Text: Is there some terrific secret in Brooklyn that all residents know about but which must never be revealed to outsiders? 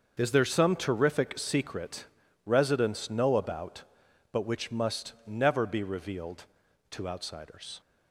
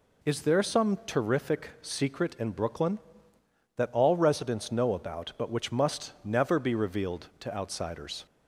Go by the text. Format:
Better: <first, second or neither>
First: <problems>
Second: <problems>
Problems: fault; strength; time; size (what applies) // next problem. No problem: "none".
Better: second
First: starts louder than the rest; until 1.1 s; 6.5 dB // skips "in Brooklyn that all"; at 2.2 s // pauses between "must" and "never"; slight; at 5.1 s; 0.16 s long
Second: none